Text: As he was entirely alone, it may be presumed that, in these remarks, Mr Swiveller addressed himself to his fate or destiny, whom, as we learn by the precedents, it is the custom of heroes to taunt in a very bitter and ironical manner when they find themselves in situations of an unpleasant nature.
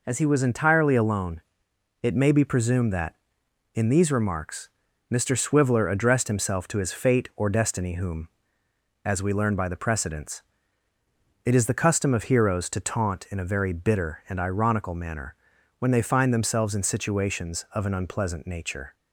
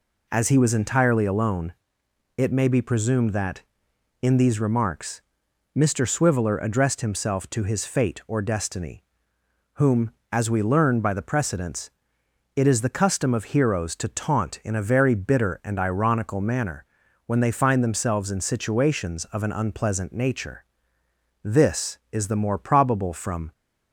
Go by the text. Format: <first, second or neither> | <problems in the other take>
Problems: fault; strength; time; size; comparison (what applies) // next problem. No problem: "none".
first | pauses between "manner" and "when"; at 16.8 s; 0.42 s long; also in the first // goes on to say "This is the more probable from"; strong; from 21.4 s on; 2.0 s long